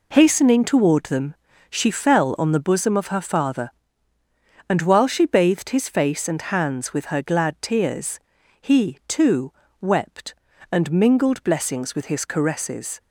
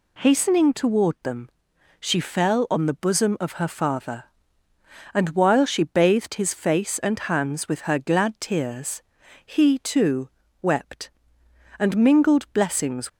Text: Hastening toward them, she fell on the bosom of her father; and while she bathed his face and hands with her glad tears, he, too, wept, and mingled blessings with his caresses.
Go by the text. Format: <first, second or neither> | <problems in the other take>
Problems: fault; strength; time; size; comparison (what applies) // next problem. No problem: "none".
first | stops before "with his caresses"; at 13.0 s